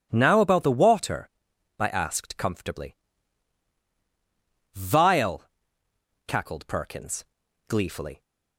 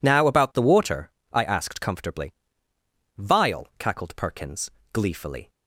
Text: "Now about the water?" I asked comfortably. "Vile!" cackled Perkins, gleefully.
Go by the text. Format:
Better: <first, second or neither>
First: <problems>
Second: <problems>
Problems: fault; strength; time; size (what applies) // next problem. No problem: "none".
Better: neither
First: none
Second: none